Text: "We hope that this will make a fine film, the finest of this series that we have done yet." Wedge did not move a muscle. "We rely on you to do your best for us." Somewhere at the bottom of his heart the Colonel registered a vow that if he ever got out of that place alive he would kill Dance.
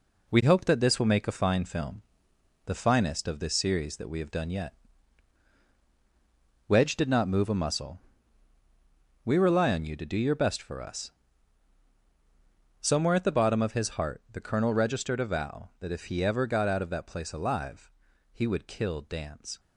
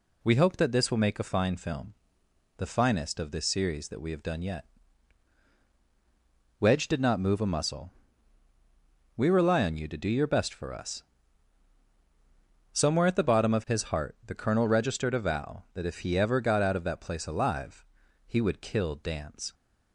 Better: second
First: gets quieter; noticeable; throughout; 5.5 dB // pauses between "alive" and "he"; at 17.8 s; 0.44 s long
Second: pauses between "alive" and "he"; at 17.8 s; 0.44 s long

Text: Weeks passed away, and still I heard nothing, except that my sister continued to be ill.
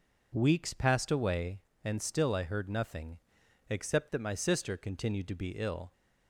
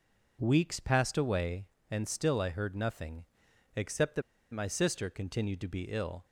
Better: first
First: none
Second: pauses between "that" and "my"; slight; at 4.2 s; 0.30 s long

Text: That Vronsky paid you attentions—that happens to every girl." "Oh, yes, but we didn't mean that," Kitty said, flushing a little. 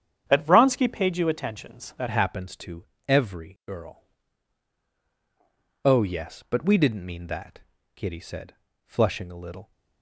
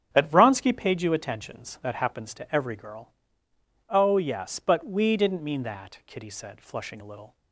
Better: second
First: starts louder than the rest; strong; until 1.2 s; 8.5 dB // changes voice at "happens"; from 2.1 s on; 7.6 s long // pauses between "to" and "every"; slight; at 2.8 s; 0.24 s long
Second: starts louder than the rest; strong; until 1.1 s; 7.5 dB

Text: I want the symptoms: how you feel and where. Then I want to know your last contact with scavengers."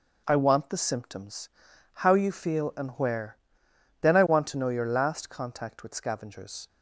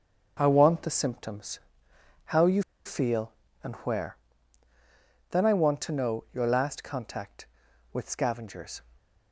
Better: first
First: starts louder than the rest; noticeable; until 1.2 s; 6 dB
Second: starts louder than the rest; until 1.4 s; 6.5 dB // pauses between "you" and "feel"; slight; at 2.6 s; 0.23 s long

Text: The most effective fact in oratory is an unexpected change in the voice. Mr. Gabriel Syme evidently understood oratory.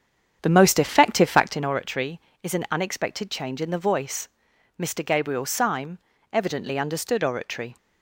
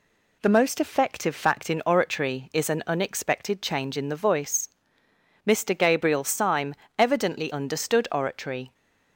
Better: second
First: starts louder than the rest; strong; until 1.7 s; 8.5 dB // pauses between "Syme" and "evidently"; slight; at 5.9 s; 0.34 s long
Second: pauses between "Syme" and "evidently"; slight; at 6.7 s; 0.20 s long

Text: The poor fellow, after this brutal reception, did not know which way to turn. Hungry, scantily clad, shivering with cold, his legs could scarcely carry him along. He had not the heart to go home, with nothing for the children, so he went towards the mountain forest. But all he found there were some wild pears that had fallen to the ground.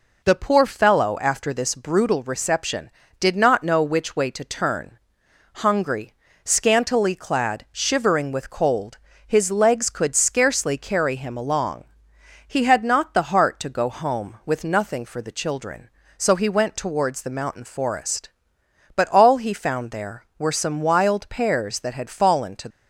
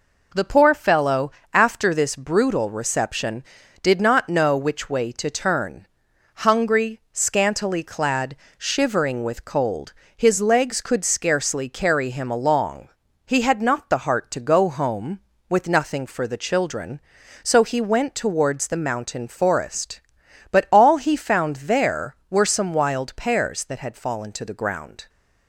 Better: second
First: stops before "the ground"; at 22.7 s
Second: none

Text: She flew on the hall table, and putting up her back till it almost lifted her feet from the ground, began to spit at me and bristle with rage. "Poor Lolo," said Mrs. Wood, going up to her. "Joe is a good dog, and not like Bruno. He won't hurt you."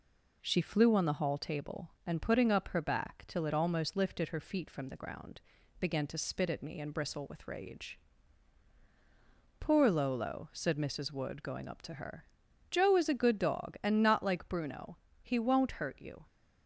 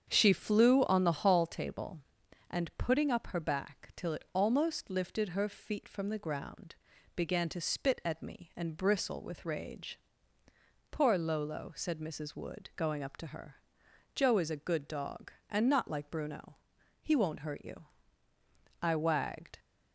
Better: first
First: none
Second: starts louder than the rest; strong; until 1.1 s; 8 dB // goes on to say "I wagged"; noticeable; from 18.8 s on; 0.78 s long

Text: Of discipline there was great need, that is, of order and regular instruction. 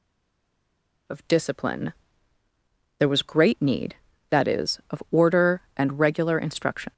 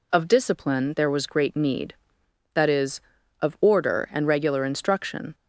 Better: second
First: stays silent before the first word; until 1.0 s; 1.0 s long // pauses between "discipline" and "there"; at 1.9 s; 1.0 s long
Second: none

